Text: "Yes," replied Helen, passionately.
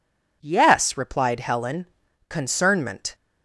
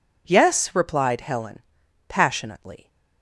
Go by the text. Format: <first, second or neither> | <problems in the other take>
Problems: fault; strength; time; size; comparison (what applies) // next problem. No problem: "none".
second | says "concernment" for "passionately"; at 2.2 s